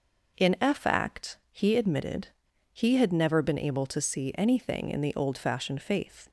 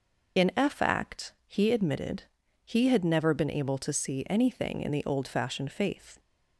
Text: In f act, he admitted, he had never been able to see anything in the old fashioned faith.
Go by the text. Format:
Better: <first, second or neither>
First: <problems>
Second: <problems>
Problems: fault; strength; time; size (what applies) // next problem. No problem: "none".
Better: first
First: none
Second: loses the start of "In"; at 0.3 s; 50 ms